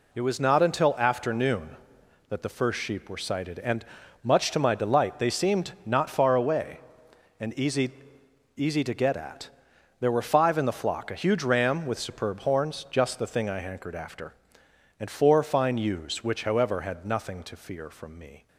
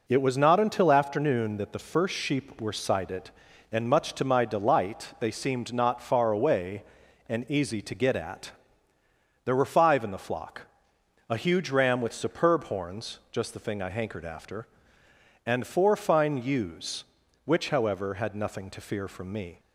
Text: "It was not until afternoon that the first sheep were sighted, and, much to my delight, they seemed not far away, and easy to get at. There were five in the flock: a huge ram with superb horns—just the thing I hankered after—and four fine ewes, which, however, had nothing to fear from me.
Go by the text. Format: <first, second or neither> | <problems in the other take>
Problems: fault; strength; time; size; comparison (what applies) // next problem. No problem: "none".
second | says "easy" twice; at 8.5 s